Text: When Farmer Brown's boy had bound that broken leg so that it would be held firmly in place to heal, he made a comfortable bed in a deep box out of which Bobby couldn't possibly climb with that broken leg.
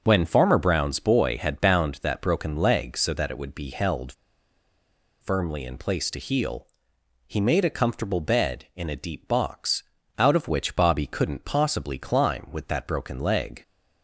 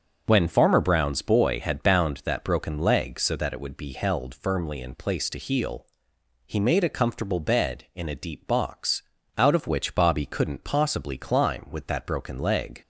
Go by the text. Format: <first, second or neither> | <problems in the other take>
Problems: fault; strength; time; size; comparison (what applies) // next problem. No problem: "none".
second | starts louder than the rest; until 1.0 s; 6.5 dB; also in the second // pauses between "held" and "firmly"; at 4.1 s; 1.0 s long // pauses between "box" and "out"; slight; at 9.8 s; 0.34 s long; slight in the second